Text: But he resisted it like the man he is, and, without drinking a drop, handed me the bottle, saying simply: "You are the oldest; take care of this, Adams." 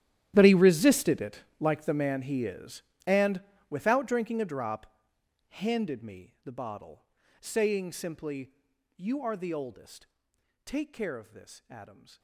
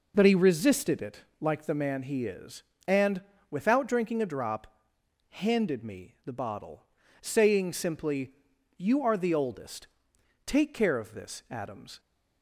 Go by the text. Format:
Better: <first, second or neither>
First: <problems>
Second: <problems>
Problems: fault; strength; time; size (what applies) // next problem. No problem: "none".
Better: second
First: gets quieter; strong; throughout; 18.5 dB // pauses between "it" and "like"; slight; at 1.3 s; 0.22 s long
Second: pauses between "it" and "like"; slight; at 1.1 s; 0.22 s long